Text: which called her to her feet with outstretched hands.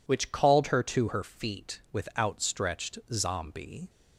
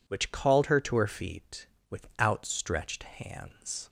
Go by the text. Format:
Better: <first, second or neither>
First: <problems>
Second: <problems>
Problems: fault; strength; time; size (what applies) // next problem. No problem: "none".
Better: second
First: says "zombie" for "hands"; at 3.1 s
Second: none